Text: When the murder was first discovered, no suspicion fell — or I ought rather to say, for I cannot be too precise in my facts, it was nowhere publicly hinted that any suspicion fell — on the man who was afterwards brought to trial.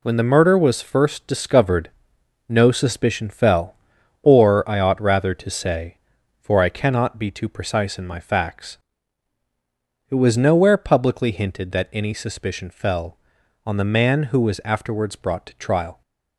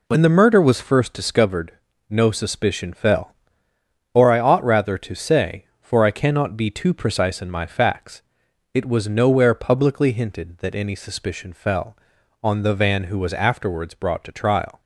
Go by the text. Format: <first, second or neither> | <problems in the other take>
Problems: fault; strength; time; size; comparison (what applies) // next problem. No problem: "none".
first | says "van" for "man"; at 12.7 s